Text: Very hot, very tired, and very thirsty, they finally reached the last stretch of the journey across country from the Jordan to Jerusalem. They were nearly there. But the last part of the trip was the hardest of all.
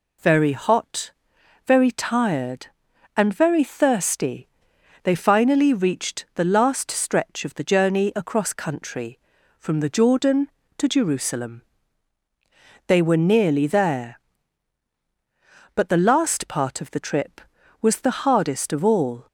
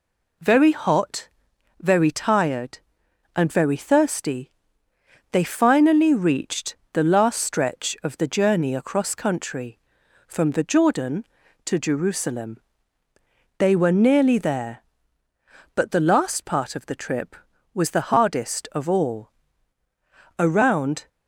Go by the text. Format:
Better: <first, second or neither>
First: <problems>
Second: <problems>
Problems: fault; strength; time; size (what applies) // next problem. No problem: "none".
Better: first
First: none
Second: pauses between "reached" and "the"; slight; at 6.7 s; 0.16 s long // goes on to say "Around"; noticeable; from 20.3 s on; 0.70 s long